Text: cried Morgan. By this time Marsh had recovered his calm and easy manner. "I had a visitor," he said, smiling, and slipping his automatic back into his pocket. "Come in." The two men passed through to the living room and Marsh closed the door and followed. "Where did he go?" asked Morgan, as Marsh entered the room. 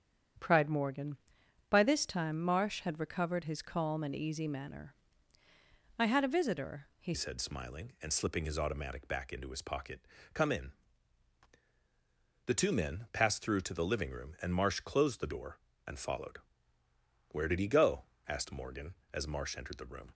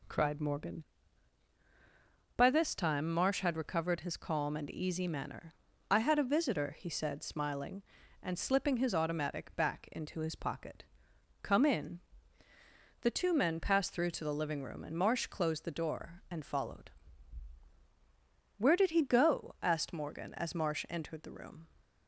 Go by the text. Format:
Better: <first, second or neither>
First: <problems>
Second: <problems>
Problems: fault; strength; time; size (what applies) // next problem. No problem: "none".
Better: second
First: starts louder than the rest; strong; until 1.9 s; 8.5 dB // changes voice at "said"; from 7.1 s on; 13.0 s long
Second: none